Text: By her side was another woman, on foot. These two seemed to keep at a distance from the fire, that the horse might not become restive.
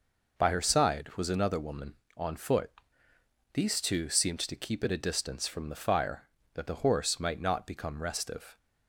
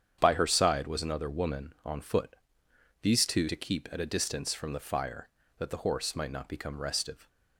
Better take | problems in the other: first | starts louder than the rest; strong; until 1.2 s; 8.5 dB // skips "seemed"; at 3.4 s

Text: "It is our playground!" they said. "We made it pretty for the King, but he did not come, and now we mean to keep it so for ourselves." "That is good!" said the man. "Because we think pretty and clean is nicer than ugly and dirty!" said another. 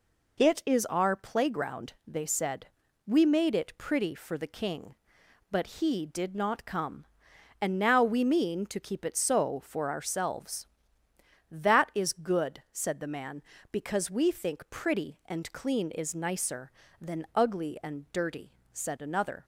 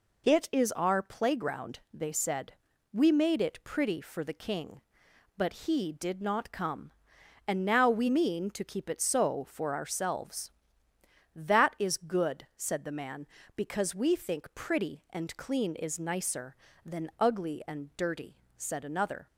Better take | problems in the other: neither | none

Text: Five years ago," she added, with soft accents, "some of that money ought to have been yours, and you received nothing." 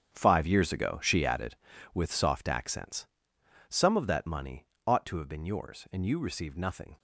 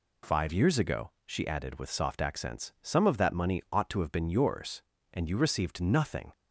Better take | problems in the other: second | gets quieter; strong; throughout; 13 dB // pauses between "money" and "ought"; slight; at 4.6 s; 0.20 s long

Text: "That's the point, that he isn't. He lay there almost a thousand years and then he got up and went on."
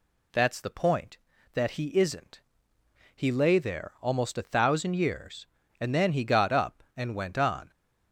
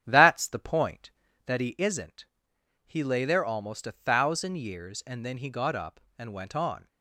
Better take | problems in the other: first | starts louder than the rest; strong; until 1.5 s; 9.5 dB

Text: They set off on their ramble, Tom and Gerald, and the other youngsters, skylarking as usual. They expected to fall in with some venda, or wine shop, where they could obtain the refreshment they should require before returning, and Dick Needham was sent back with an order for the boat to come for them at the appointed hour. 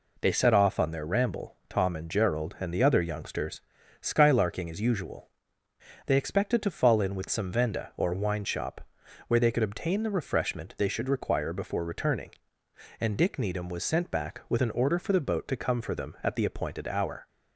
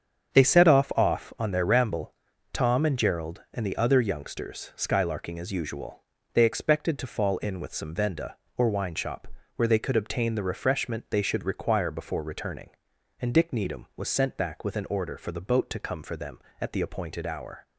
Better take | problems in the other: first | starts louder than the rest; strong; until 1.4 s; 7.5 dB // says "off" twice; at 0.9 s

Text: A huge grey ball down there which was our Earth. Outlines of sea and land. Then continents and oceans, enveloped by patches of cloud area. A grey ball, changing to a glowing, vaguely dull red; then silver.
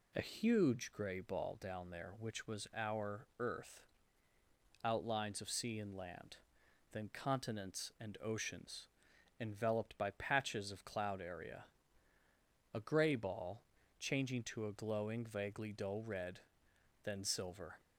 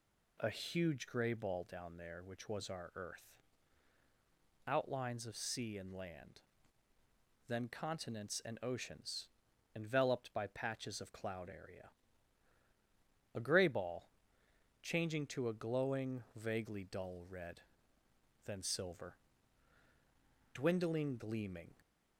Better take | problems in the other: first | goes on to say "Dwindling gleaming"; noticeable; from 20.5 s on; 1.2 s long

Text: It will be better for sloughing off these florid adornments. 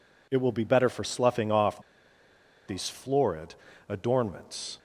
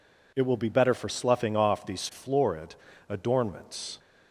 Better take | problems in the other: second | pauses between "off" and "these"; noticeable; at 1.7 s; 0.88 s long // pauses between "florid" and "adornments"; slight; at 3.5 s; 0.34 s long; slight in the second

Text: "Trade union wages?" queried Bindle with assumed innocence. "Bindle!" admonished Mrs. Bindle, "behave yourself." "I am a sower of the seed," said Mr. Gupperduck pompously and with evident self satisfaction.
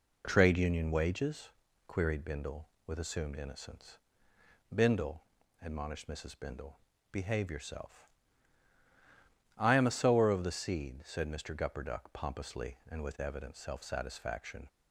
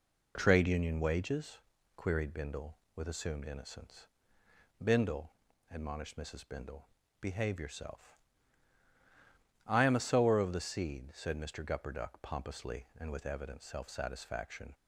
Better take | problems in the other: neither | none

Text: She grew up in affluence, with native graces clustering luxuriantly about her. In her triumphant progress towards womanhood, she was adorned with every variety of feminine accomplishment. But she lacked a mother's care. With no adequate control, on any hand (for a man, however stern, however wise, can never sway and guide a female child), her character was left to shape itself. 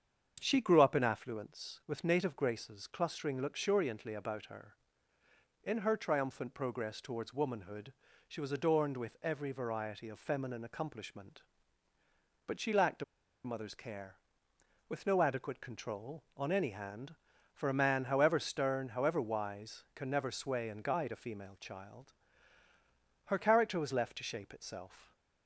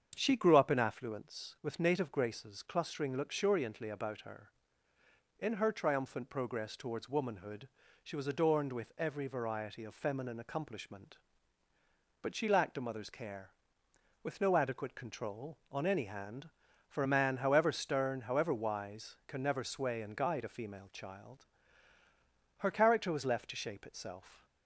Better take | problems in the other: second | starts louder than the rest; strong; until 1.4 s; 7.5 dB; strong in the second // pauses between "a" and "mother's"; at 13.0 s; 0.40 s long

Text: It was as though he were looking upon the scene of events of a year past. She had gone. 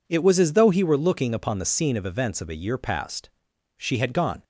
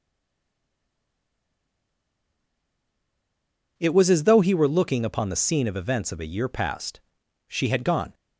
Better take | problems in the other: first | stays silent before the first word; strong; until 3.7 s; 3.7 s long

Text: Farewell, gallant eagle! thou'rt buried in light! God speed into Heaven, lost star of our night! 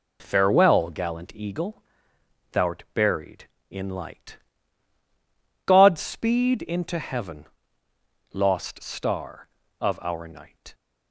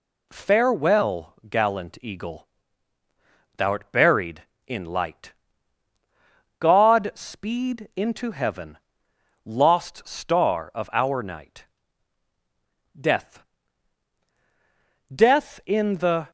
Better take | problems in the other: first | goes on to say "Death Death in the"; strong; from 12.9 s on; 3.3 s long

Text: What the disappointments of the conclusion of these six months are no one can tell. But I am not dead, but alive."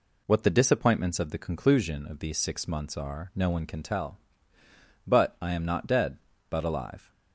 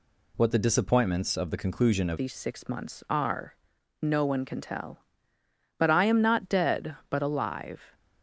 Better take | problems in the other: first | changes voice at "these"; from 2.1 s on; 5.8 s long // pauses between "are" and "no"; noticeable; at 3.5 s; 0.46 s long

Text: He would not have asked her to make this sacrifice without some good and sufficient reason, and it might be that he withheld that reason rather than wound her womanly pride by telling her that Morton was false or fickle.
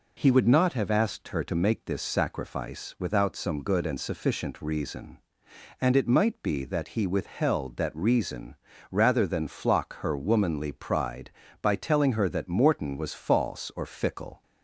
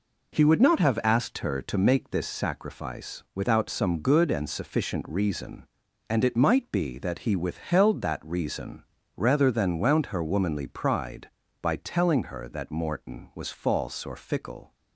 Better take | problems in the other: second | pauses between "reason" and "rather"; slight; at 8.5 s; 0.34 s long; slight in the second // says "flock" for "wound"; at 9.4 s

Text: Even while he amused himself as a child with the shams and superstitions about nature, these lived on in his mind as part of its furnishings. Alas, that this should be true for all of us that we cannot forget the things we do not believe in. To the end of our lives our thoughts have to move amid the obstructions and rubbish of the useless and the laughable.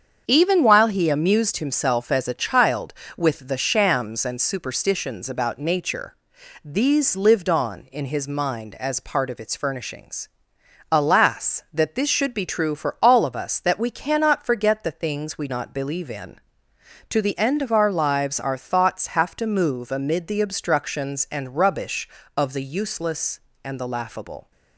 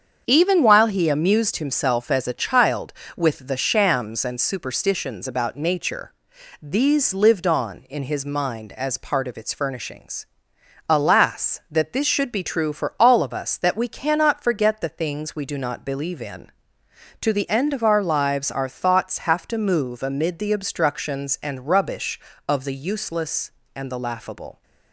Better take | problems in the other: second | starts louder than the rest; strong; until 1.2 s; 7 dB; strong in the second // skips "do"; at 15.4 s

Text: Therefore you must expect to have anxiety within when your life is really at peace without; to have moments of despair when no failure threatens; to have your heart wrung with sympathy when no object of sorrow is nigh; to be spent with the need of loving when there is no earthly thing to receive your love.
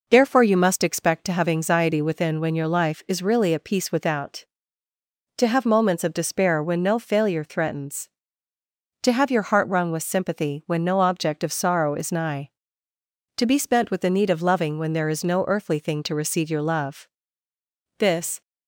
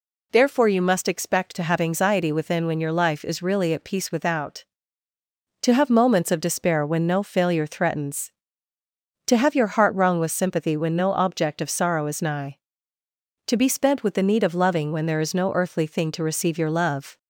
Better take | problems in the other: second | goes on to say "This"; slight; from 17.9 s on; 0.44 s long

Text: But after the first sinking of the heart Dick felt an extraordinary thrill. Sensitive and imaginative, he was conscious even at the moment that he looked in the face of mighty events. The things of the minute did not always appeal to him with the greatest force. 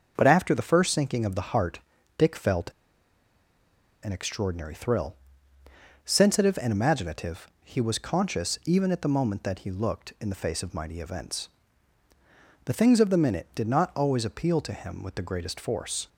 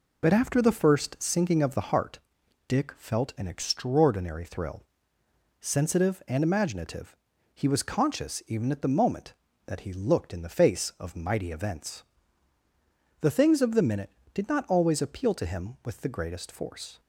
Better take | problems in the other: second | starts louder than the rest; until 1.1 s; 6.5 dB // pauses between "heart" and "Dick"; at 1.7 s; 0.40 s long; noticeable in the second // pauses between "felt" and "an"; strong; at 2.7 s; 1.3 s long

